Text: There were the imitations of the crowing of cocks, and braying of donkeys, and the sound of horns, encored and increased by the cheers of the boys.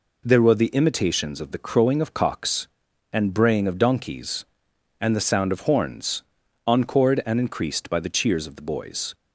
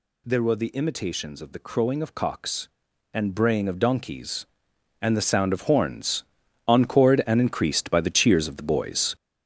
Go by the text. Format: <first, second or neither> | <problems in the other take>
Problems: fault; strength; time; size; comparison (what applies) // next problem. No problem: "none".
first | gets louder; strong; throughout; 7.5 dB